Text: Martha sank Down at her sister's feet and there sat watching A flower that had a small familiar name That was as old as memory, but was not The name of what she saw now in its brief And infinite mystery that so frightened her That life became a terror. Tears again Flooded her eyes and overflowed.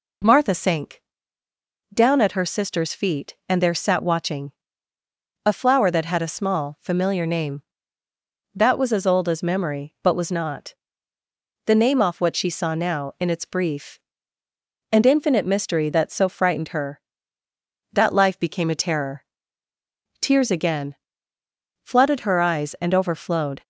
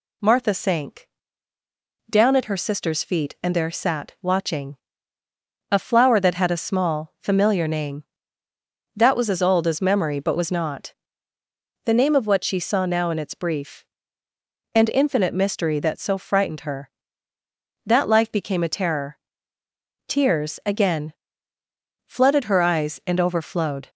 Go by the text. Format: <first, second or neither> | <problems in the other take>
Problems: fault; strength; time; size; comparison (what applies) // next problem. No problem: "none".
second | pauses between "sank" and "Down"; noticeable; at 1.0 s; 0.92 s long; also in the second // pauses between "watching" and "A"; noticeable; at 4.5 s; 0.92 s long; noticeable in the second // pauses between "not" and "The"; noticeable; at 10.7 s; 0.90 s long; noticeable in the second // says "off" for "of"; at 12.0 s // pauses between "again" and "Flooded"; noticeable; at 20.9 s; 0.88 s long; noticeable in the second